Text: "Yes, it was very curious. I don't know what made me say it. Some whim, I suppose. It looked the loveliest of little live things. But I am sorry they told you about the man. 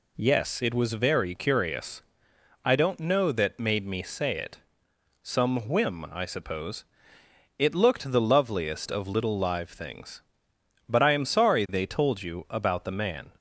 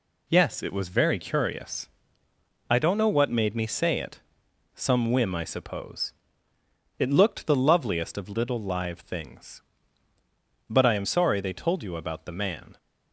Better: second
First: says "that" for "what"; at 3.3 s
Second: none

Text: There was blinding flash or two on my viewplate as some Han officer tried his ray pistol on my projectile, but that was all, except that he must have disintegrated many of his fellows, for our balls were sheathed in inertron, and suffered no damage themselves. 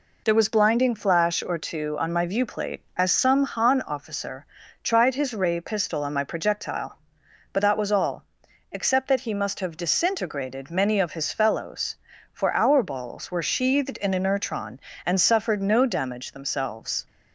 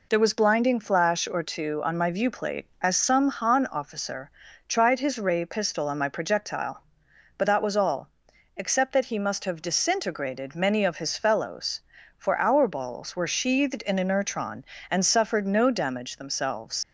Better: first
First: pauses between "officer" and "tried"; at 4.4 s; 0.40 s long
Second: pauses between "officer" and "tried"; at 4.2 s; 0.40 s long // leaves "themselves" unfinished; at 16.8 s; 75 ms

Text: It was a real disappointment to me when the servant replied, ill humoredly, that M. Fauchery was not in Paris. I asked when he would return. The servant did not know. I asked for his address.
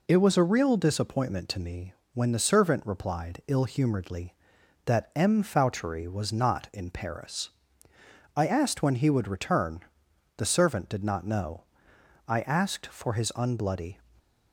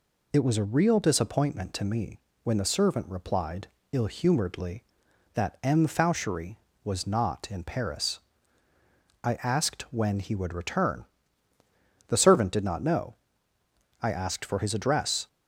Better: second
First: pauses between "me" and "when"; slight; at 1.9 s; 0.22 s long // says "unbloody" for "address"; at 13.3 s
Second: pauses between "me" and "when"; slight; at 2.2 s; 0.22 s long

